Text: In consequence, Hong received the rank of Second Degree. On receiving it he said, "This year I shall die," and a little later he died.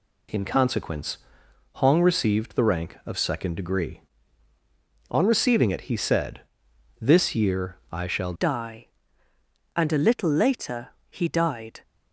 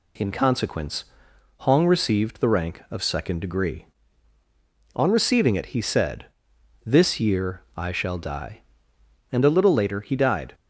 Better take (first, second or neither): second